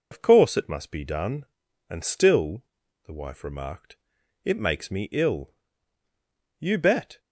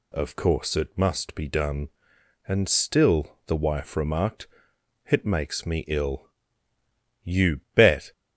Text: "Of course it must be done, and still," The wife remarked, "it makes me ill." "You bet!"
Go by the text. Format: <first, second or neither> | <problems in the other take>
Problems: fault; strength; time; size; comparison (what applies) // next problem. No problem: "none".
second | loses the start of "Of"; at 0.1 s; 55 ms